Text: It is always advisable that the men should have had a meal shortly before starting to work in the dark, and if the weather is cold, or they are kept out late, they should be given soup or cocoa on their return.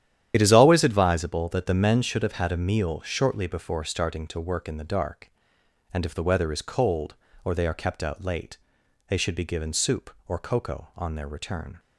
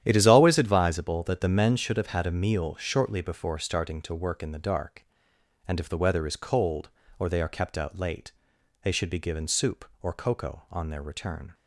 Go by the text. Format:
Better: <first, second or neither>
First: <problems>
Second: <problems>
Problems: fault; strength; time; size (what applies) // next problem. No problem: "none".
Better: second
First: loses the start of "It"; at 0.3 s; 55 ms // starts louder than the rest; strong; until 1.3 s; 10.5 dB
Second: starts louder than the rest; strong; until 1.0 s; 11 dB